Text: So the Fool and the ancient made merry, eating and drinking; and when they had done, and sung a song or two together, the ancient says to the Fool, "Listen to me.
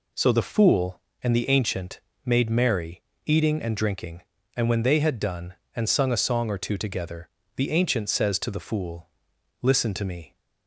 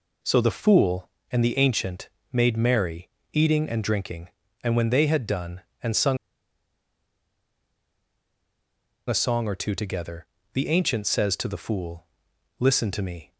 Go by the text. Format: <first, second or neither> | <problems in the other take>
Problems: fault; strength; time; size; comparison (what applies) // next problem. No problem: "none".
first | pauses between "ancient" and "made"; slight; at 2.0 s; 0.22 s long; slight in the first // pauses between "sung" and "a"; strong; at 6.1 s; 2.9 s long